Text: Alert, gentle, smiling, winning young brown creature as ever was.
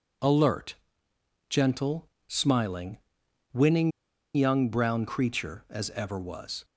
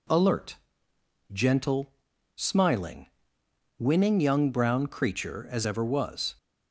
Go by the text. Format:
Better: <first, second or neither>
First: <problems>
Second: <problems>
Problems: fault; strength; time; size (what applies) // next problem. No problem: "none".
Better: second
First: pauses between "winning" and "young"; at 3.9 s; 0.43 s long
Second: none